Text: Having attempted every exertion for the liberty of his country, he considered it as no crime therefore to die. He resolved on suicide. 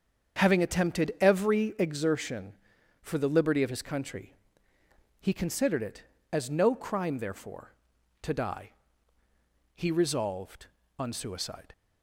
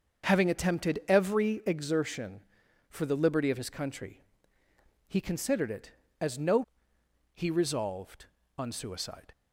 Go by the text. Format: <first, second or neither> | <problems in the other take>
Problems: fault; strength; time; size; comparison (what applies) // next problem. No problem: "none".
first | starts louder than the rest; until 1.3 s; 7 dB; strong in the first // skips "crime therefore to die"; at 6.9 s